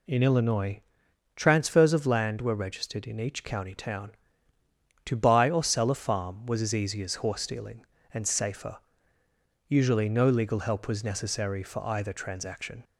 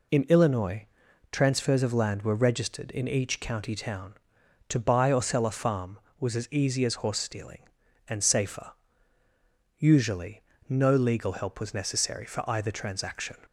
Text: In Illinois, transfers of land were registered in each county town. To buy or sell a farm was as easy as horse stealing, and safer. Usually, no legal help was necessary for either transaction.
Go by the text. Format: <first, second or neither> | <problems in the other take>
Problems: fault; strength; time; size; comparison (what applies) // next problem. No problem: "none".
neither | none